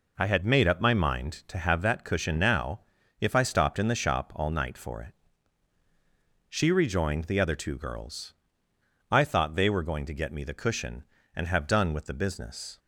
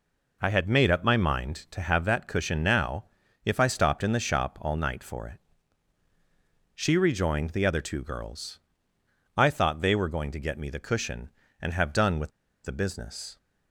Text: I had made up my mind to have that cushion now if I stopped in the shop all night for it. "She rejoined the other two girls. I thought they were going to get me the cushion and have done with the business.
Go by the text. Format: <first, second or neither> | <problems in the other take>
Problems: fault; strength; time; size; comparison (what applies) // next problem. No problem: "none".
first | pauses between "now" and "if"; at 3.0 s; 0.40 s long; also in the first // pauses between "with" and "the"; slight; at 12.3 s; 0.33 s long